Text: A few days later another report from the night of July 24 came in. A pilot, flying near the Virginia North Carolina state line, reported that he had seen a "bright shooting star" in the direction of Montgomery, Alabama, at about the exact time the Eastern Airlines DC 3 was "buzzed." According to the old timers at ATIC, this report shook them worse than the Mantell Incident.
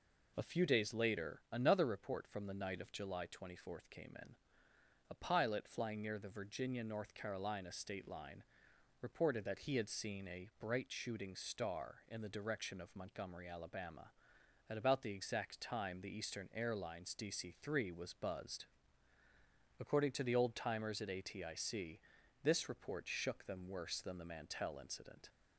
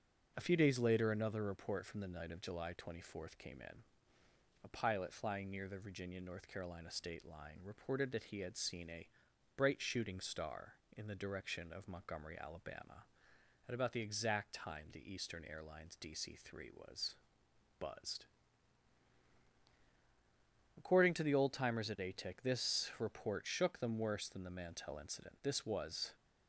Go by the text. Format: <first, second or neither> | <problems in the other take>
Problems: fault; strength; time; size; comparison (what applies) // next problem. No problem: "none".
first | starts louder than the rest; until 1.3 s; 6.5 dB // pauses between "a" and "bright"; noticeable; at 9.0 s; 0.50 s long // pauses between "was" and "buzzed"; noticeable; at 17.1 s; 0.64 s long // goes on to say "This was"; noticeable; from 25.4 s on; 0.72 s long